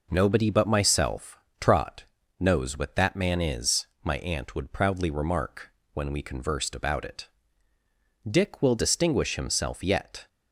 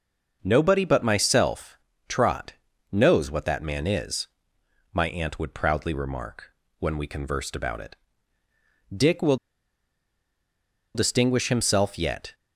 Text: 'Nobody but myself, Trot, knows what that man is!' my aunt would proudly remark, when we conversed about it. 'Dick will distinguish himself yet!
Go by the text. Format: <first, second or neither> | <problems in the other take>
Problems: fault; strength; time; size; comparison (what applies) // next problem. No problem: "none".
first | pauses between "will" and "distinguish"; strong; at 9.3 s; 1.5 s long